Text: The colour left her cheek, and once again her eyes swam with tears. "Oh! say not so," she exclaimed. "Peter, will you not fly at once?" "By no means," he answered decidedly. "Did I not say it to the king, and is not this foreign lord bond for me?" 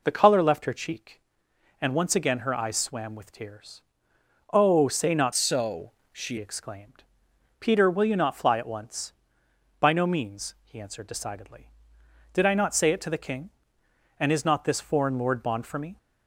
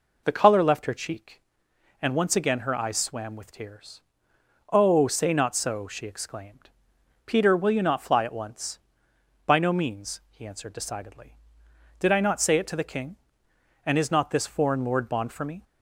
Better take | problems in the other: second | changes voice from "so" to "she"; from 5.3 to 6.3 s; 1.0 s long

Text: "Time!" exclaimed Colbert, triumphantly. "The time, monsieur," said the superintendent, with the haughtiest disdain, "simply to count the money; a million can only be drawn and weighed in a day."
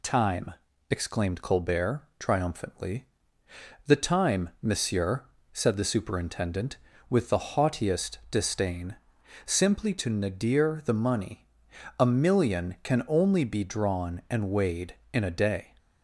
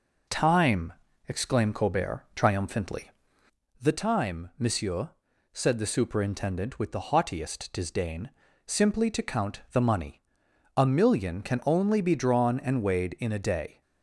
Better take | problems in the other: second | says "nadir" for "count"; at 10.1 s

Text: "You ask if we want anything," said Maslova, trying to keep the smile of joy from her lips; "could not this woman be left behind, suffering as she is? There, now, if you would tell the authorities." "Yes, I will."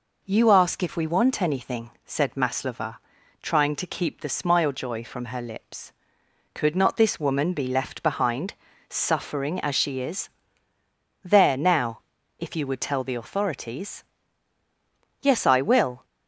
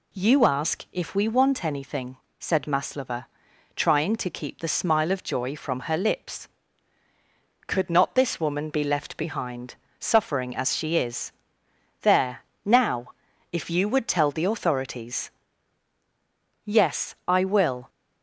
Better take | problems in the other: second | skips "of"; at 4.7 s

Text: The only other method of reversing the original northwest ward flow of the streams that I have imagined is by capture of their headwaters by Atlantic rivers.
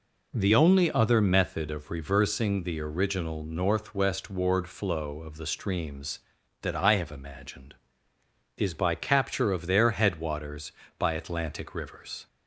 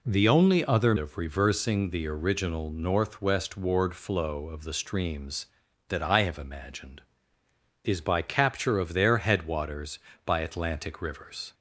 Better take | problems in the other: first | skips "method"; at 0.9 s

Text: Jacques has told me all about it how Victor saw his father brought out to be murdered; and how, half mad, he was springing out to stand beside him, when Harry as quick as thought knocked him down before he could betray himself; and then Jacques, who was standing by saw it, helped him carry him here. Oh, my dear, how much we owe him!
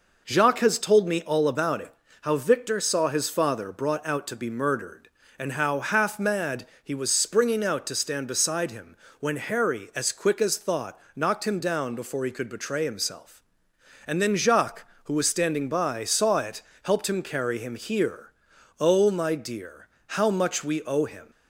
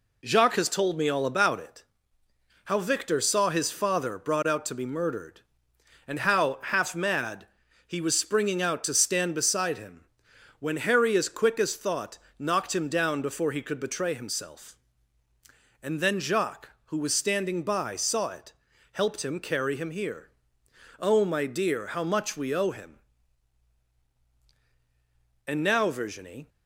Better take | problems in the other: first | pauses between "it" and "how"; noticeable; at 1.8 s; 0.82 s long; slight in the first // pauses between "thought" and "knocked"; slight; at 12.1 s; 0.18 s long; slight in the first // goes on to say "And now Virginie"; noticeable; from 25.4 s on; 1.0 s long

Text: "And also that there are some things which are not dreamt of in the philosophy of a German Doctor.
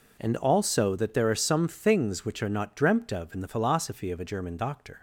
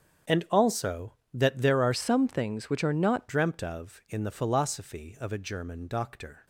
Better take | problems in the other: first | starts louder than the rest; strong; until 1.5 s; 8 dB // changes voice from "some" to "not"; from 1.9 to 3.2 s; 1.3 s long

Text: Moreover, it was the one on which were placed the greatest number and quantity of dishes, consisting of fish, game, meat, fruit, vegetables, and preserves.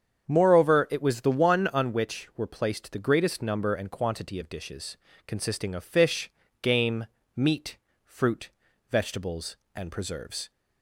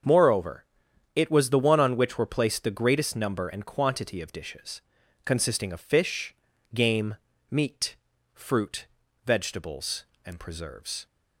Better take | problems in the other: neither | starts louder than the rest; the same in both

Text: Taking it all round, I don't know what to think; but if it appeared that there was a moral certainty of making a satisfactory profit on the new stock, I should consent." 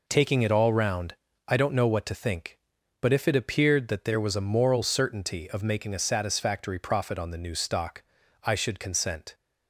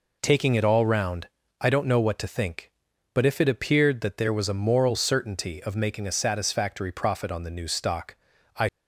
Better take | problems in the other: first | stops before "should consent"; at 8.6 s

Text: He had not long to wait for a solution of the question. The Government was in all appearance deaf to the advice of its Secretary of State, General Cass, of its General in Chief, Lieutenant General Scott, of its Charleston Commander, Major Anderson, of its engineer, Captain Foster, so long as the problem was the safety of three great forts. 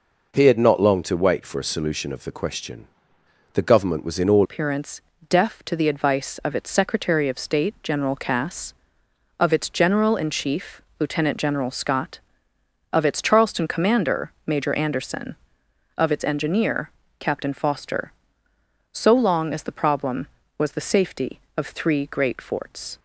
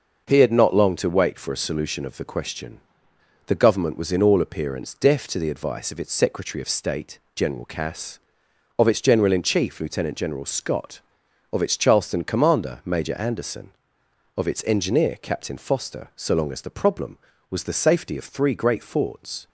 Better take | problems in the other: second | changes voice at "appearance"; from 4.4 s on; 18.5 s long // pauses between "appearance" and "deaf"; slight; at 5.0 s; 0.28 s long

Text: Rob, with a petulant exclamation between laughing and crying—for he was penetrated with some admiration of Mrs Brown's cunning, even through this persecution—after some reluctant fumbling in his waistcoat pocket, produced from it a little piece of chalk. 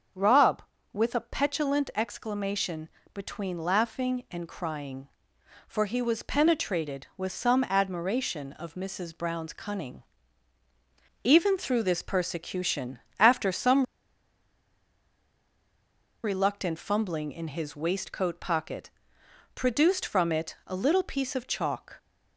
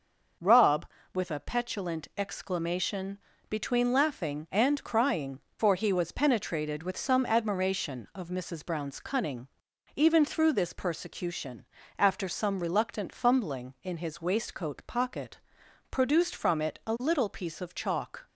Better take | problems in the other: second | starts louder than the rest; until 1.4 s; 7 dB; noticeable in the second // pauses between "exclamation" and "between"; slight; at 2.8 s; 0.24 s long; slight in the second // pauses between "some" and "reluctant"; strong; at 13.8 s; 2.3 s long

